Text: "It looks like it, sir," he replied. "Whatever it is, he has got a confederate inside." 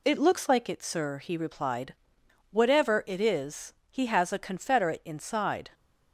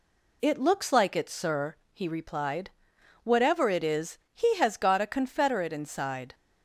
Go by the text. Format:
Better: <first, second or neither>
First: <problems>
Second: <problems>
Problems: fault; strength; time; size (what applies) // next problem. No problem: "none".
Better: second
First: skips "got"; at 4.3 s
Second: none